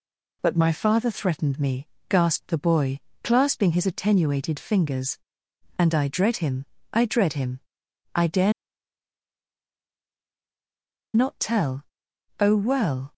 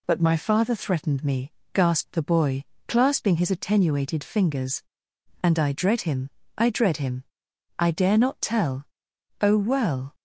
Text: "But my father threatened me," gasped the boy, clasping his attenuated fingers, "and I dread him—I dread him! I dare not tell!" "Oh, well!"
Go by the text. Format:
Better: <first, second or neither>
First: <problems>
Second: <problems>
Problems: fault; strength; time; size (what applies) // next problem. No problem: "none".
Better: second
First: pauses between "dare" and "not"; strong; at 8.5 s; 2.6 s long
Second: none